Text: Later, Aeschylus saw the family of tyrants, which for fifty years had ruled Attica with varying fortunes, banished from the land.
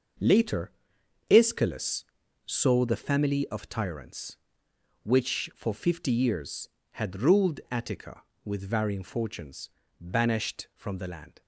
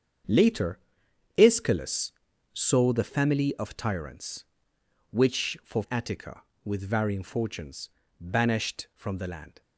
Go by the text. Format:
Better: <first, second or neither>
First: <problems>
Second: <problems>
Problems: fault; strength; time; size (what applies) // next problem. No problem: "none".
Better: first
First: starts louder than the rest; until 1.7 s; 6.5 dB // pauses between "Aeschylus" and "saw"; at 2.0 s; 0.42 s long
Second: starts louder than the rest; strong; until 1.8 s; 7.5 dB // pauses between "Aeschylus" and "saw"; at 2.1 s; 0.42 s long // skips "fifty years had ruled"; at 5.8 s